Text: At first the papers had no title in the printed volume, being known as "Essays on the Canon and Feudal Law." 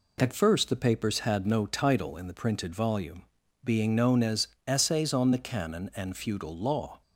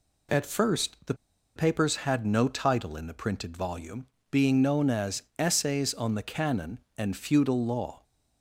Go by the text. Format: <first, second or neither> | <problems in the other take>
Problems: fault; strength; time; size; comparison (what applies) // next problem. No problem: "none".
first | pauses between "the" and "papers"; at 1.1 s; 0.41 s long // pauses between "as" and "Essays"; slight; at 5.2 s; 0.16 s long; slight in the first